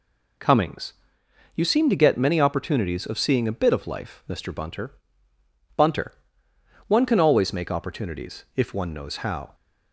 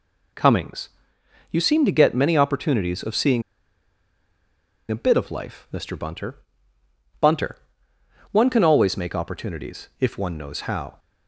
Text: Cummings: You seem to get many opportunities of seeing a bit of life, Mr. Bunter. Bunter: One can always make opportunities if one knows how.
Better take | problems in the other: first | pauses between "seeing" and "a"; strong; at 3.4 s; 1.4 s long

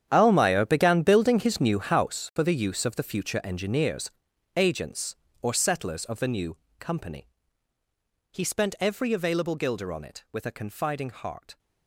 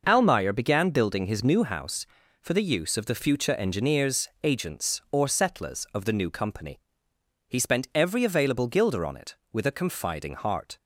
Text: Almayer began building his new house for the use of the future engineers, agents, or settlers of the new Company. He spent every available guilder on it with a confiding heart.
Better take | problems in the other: second | gets quieter; strong; throughout; 15.5 dB // pauses between "new" and "Company"; slight; at 6.5 s; 0.22 s long

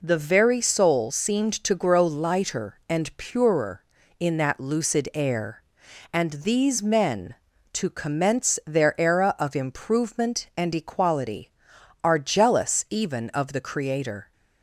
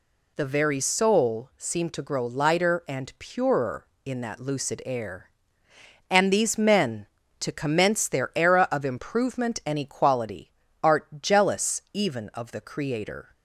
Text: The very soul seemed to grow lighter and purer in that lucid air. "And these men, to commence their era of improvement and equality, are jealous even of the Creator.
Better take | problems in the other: first | says "art" for "are"; at 10.8 s

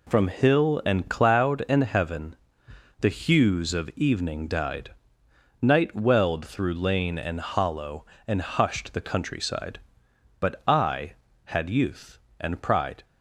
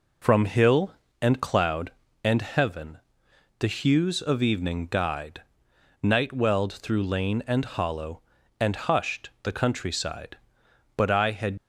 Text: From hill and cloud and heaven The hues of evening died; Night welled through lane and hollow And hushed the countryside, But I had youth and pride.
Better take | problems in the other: first | pauses between "heaven" and "The"; noticeable; at 2.9 s; 0.60 s long; noticeable in the first // stops before "youth and pride"; at 11.5 s

